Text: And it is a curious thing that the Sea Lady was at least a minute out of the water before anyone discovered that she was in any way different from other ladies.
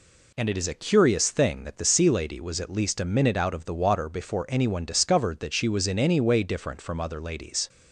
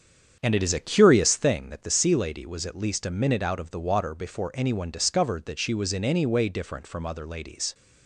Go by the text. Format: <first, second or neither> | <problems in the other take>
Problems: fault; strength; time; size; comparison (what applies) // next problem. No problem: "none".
first | starts louder than the rest; strong; until 1.6 s; 7.5 dB